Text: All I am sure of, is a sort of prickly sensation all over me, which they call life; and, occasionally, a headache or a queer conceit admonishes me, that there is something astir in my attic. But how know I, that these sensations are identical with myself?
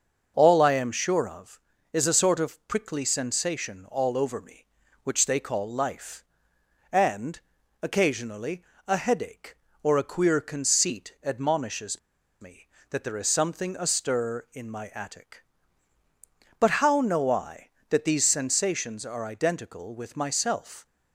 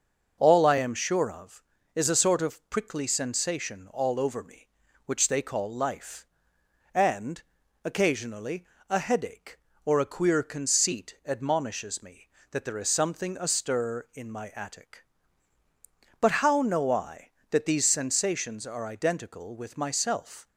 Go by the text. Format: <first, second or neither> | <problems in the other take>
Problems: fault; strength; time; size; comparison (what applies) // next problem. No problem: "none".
second | starts louder than the rest; until 1.3 s; 6.5 dB; noticeable in the second // pauses between "admonishes" and "me"; at 11.9 s; 0.41 s long